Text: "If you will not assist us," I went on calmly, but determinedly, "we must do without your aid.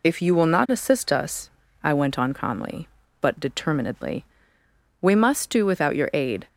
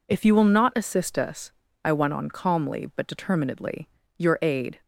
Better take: first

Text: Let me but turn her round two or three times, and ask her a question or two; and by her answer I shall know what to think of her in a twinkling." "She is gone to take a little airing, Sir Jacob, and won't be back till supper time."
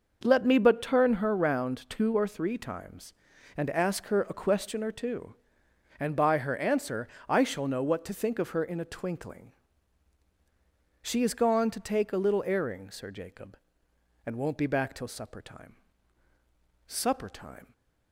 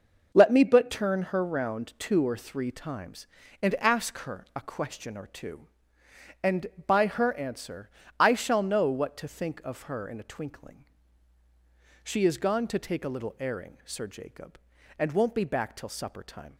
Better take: second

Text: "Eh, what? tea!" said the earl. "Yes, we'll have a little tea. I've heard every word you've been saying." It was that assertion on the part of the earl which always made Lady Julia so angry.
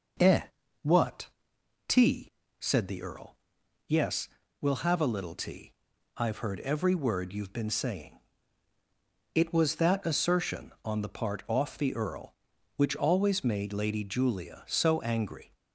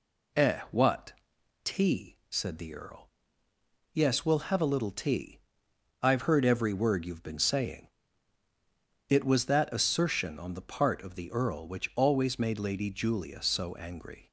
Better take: second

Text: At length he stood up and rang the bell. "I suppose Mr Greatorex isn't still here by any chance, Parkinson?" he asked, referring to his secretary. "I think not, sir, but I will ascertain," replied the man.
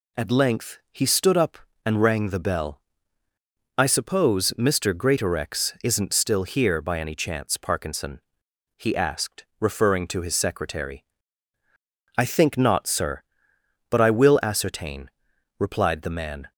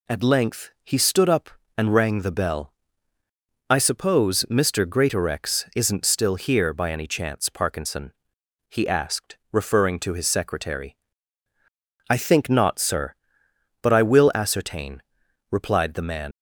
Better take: first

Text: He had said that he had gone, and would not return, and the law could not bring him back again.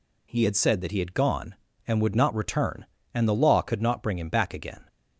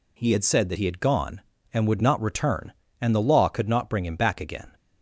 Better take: neither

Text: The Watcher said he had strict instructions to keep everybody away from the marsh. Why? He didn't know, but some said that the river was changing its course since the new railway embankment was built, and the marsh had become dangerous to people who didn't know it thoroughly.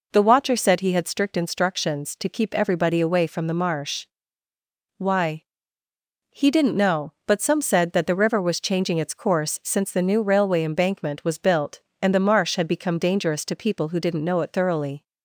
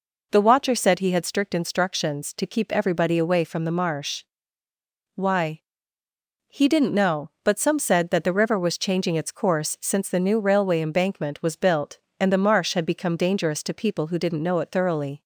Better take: neither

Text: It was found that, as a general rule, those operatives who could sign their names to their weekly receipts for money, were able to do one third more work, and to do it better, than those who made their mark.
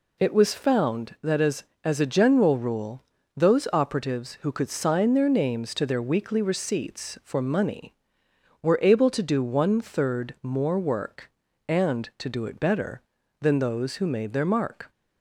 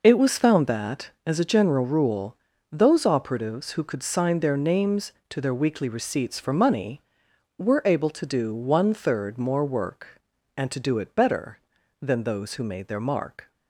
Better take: second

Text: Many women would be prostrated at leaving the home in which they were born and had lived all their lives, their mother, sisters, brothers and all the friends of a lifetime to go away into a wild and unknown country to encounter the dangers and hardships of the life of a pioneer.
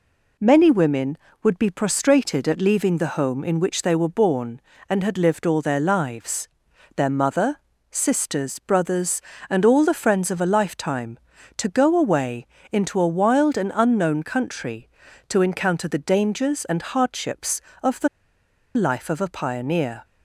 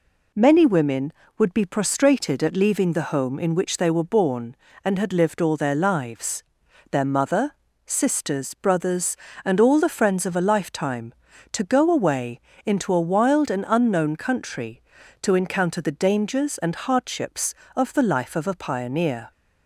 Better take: second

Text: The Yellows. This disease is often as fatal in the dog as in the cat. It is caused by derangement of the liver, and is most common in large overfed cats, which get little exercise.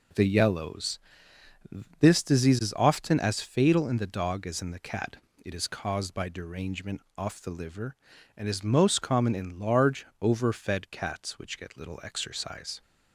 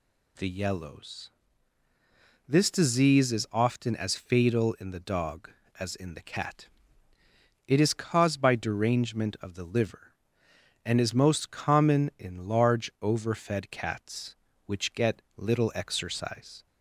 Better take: second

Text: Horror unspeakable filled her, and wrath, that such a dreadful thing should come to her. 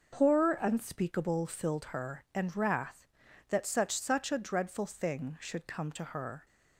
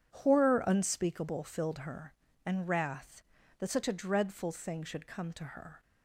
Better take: second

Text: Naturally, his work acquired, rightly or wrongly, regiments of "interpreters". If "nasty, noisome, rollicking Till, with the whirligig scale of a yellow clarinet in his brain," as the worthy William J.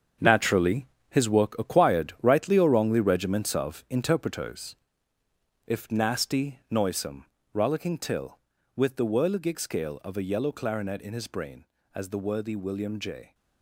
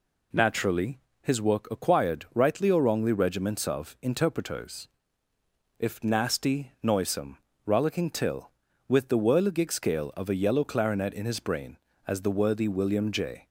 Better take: second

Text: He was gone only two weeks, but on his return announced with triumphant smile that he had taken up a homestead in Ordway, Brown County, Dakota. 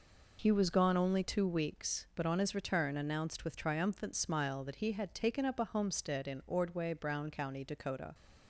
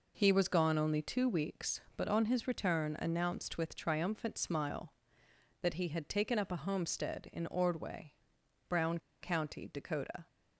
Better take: first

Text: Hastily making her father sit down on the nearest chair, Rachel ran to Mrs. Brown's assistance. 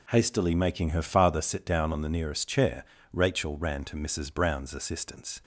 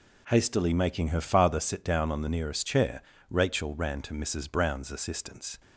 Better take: neither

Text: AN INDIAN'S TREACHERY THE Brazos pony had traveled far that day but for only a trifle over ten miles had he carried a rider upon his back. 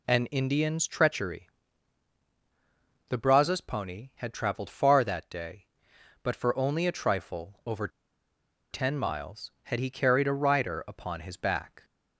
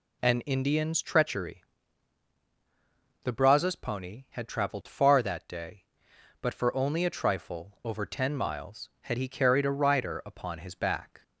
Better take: second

